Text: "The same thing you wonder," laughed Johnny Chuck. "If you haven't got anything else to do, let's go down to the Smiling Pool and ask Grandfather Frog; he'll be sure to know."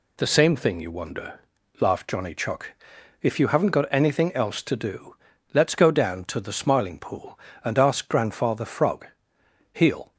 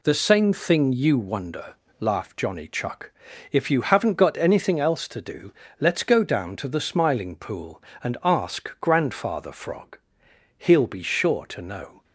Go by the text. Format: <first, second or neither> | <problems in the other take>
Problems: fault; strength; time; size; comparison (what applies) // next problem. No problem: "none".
second | stops before "be sure to know"; at 10.1 s